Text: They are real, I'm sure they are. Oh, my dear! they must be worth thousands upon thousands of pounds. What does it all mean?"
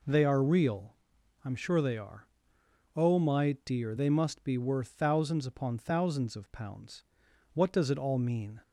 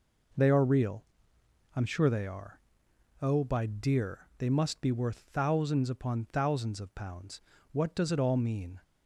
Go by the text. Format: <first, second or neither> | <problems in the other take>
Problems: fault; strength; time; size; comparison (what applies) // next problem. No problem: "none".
first | says "by" for "my"; at 3.4 s